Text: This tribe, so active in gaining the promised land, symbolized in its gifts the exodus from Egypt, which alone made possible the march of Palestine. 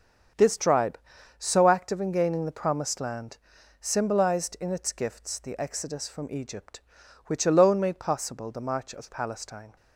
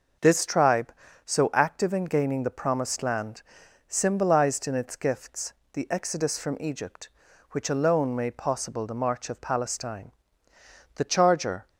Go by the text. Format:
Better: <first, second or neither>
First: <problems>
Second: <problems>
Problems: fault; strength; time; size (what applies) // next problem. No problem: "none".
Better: first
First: starts louder than the rest; until 1.7 s; 6.5 dB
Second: starts louder than the rest; noticeable; until 1.5 s; 6 dB // pauses between "gifts" and "the"; slight; at 5.5 s; 0.22 s long // goes on to say "The charger"; noticeable; from 10.9 s on; 0.74 s long